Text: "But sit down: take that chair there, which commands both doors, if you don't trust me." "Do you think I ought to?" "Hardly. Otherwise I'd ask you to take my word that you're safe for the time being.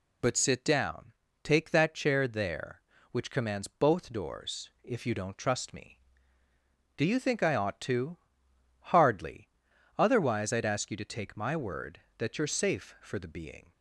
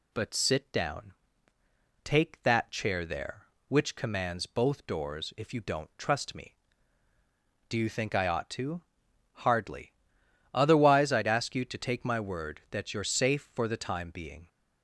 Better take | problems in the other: second | skips "time"; at 13.2 s

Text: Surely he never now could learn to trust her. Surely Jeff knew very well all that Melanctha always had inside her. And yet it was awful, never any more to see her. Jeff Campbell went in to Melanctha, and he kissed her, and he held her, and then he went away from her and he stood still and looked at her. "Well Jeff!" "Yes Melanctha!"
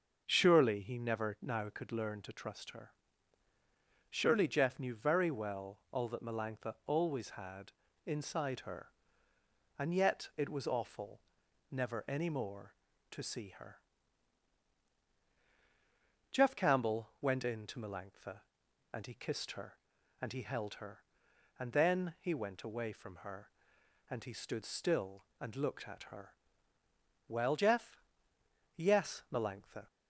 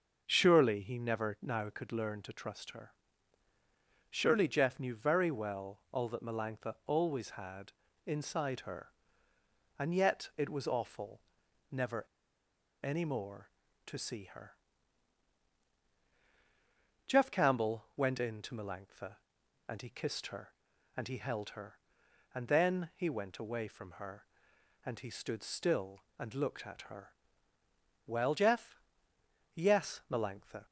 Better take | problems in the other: first | starts louder than the rest; until 1.2 s; 6 dB; also in the first // pauses between "had" and "inside"; slight; at 7.7 s; 0.34 s long; slight in the first // pauses between "never" and "any"; noticeable; at 12.0 s; 0.79 s long

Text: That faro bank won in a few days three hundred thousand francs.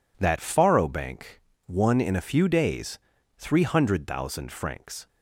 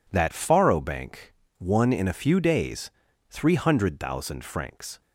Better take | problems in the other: neither | pauses between "bank" and "won"; slight; the same in both // pauses between "days" and "three"; the same in both

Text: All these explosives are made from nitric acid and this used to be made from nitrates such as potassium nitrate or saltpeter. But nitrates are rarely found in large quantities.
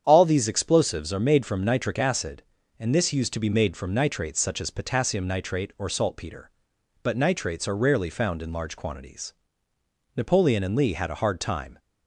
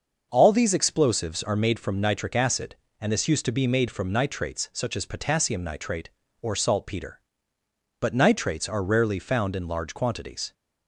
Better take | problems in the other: second | starts louder than the rest; strong; until 1.0 s; 8.5 dB; noticeable in the second // goes on to say "Napoleon and Lee had a hard time"; from 10.1 s on; 1.6 s long

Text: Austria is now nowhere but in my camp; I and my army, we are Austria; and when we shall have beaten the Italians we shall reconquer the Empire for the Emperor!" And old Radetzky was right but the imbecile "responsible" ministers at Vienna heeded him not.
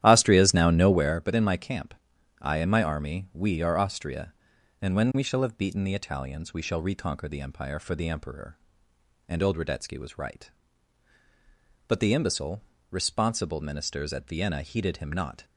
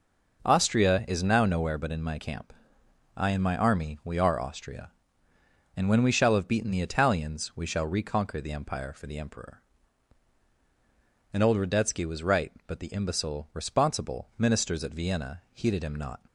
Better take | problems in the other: second | starts louder than the rest; strong; until 1.2 s; 12 dB // pauses between "imbecile" and "responsible"; slight; at 12.6 s; 0.28 s long

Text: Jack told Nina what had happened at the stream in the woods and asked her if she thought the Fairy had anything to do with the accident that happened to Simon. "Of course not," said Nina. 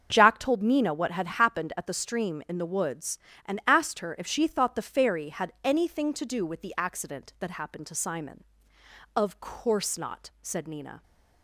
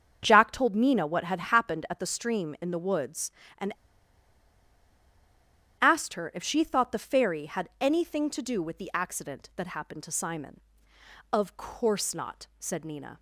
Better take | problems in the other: first | starts louder than the rest; until 1.2 s; 7 dB; also in the first // pauses between "and" and "asked"; strong; at 3.7 s; 2.0 s long

